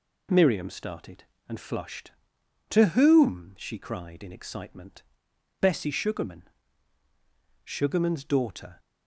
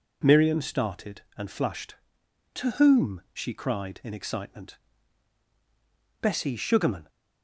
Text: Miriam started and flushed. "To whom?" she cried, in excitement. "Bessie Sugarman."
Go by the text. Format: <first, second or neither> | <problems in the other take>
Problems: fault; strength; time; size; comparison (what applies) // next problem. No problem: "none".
second | goes on to say "Sugarman's daughter"; noticeable; from 7.6 s on; 1.1 s long